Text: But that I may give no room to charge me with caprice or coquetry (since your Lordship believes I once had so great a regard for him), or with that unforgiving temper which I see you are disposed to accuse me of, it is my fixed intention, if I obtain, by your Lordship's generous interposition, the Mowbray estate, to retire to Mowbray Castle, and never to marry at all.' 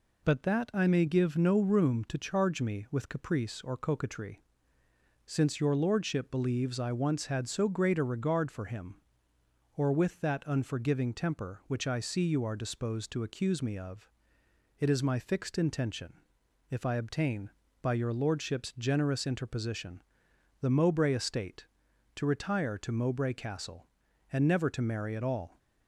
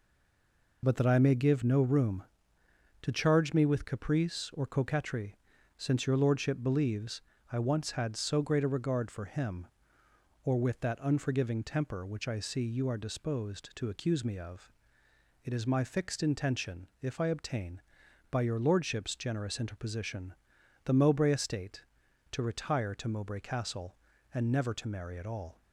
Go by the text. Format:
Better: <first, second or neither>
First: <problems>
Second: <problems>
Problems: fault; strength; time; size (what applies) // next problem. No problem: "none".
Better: first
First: none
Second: stays silent before the first word; slight; until 0.8 s; 0.8 s long // pauses between "believes" and "I"; slight; at 7.2 s; 0.28 s long